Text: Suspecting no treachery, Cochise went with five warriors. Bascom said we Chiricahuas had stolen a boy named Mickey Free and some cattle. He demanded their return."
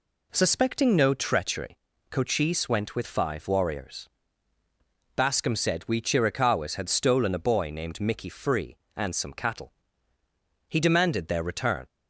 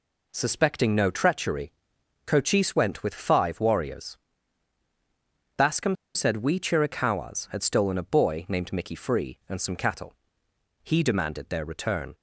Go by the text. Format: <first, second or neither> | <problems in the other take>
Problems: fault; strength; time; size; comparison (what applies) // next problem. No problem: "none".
first | pauses between "Bascom" and "said"; slight; at 5.9 s; 0.19 s long